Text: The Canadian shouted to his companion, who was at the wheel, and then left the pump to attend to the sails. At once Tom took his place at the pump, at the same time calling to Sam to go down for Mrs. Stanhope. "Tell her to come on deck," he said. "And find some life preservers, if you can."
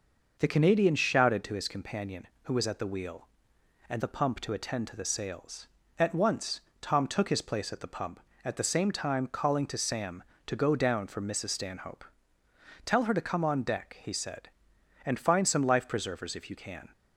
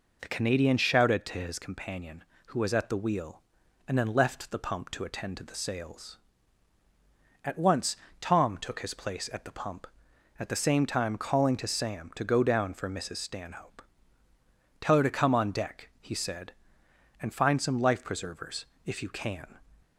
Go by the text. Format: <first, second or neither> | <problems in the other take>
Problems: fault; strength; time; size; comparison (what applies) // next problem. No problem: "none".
second | skips "then left"; at 4.0 s // pauses between "once" and "Tom"; slight; at 6.6 s; 0.20 s long; slight in the second